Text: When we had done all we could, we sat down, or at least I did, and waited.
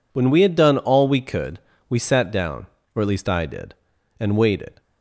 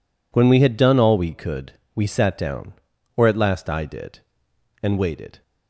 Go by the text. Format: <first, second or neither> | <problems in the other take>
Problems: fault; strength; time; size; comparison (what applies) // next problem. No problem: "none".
first | says "last" for "least"; at 3.3 s